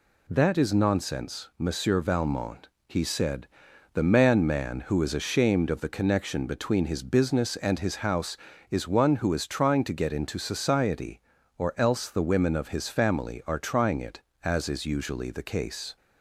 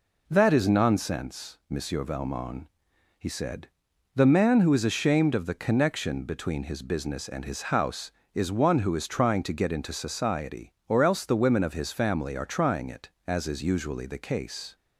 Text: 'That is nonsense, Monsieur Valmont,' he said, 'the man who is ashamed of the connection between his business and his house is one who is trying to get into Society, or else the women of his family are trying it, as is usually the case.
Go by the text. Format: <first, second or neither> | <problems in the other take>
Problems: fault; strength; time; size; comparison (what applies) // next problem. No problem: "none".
second | says "man" twice; at 4.4 s